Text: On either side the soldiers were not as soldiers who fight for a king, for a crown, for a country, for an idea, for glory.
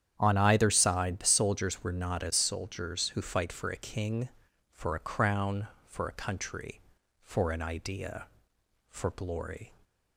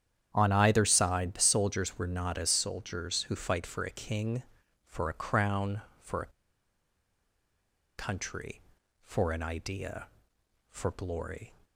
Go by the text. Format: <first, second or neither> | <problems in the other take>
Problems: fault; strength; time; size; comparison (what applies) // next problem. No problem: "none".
first | starts louder than the rest; strong; until 1.3 s; 9.5 dB; strong in the first // pauses between "a" and "country"; strong; at 6.3 s; 1.6 s long